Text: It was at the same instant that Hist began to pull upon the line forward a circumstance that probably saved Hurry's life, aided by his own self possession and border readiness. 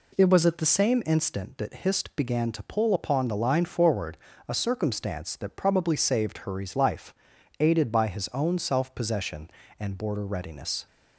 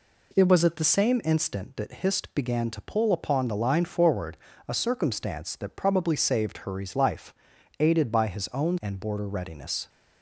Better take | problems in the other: first | pauses between "forward" and "a"; slight; at 4.3 s; 0.28 s long; slight in the first // skips "self possession"; at 8.8 s

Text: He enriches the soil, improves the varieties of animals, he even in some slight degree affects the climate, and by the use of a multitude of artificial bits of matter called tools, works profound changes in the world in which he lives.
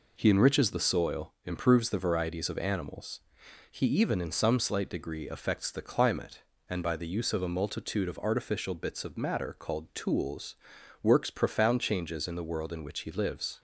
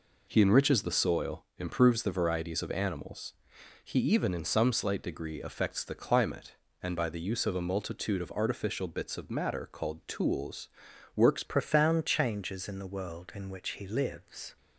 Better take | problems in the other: first | changes voice at "profound"; from 11.4 s on; 3.1 s long

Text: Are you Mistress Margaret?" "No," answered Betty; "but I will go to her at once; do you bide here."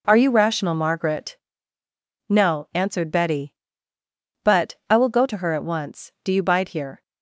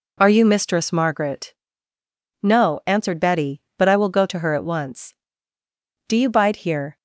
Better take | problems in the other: second | says "Rational" for "Mistress"; at 0.2 s

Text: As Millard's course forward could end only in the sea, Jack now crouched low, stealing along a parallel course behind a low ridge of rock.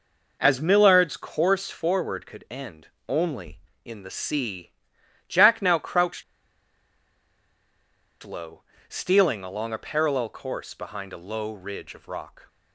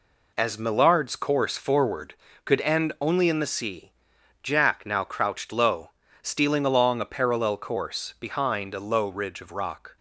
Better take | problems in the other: second | pauses between "end" and "only"; slight; at 2.8 s; 0.20 s long // pauses between "crouched" and "low"; strong; at 6.2 s; 2.0 s long

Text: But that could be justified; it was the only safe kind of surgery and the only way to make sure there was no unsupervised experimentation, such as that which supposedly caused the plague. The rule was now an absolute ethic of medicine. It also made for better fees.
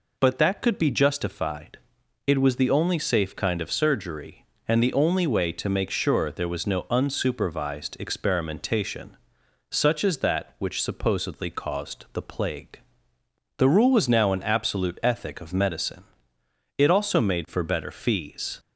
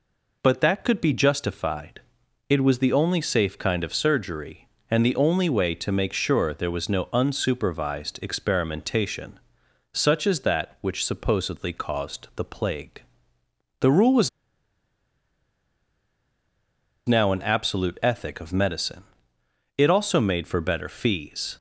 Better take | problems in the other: first | pauses between "was" and "now"; strong; at 14.2 s; 2.7 s long

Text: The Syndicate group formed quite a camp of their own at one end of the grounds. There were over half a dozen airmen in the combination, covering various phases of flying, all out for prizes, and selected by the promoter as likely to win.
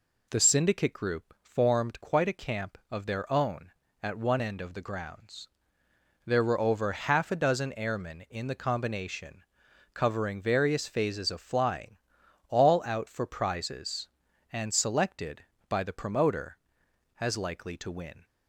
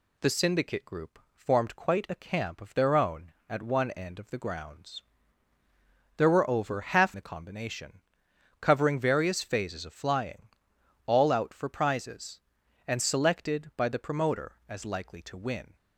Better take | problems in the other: first | pauses between "group" and "formed"; slight; at 1.1 s; 0.16 s long // skips "a dozen airmen in"; at 7.1 s

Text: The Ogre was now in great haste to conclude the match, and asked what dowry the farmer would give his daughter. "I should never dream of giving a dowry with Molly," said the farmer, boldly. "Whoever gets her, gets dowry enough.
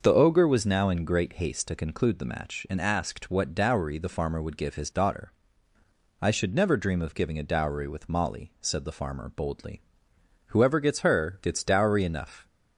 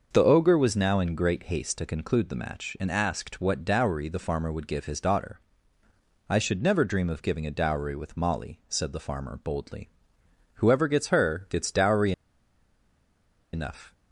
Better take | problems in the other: first | starts louder than the rest; noticeable; until 1.1 s; 6 dB; noticeable in the first // pauses between "dowry" and "enough"; strong; at 12.1 s; 1.4 s long

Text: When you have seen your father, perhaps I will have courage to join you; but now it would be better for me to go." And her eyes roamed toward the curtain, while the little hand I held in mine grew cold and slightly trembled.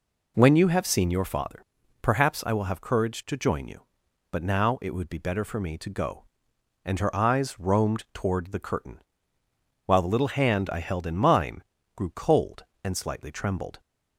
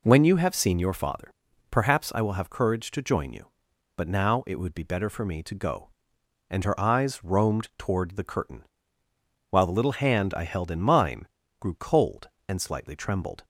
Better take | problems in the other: neither | pauses between "mine" and "grew"; slight; the same in both

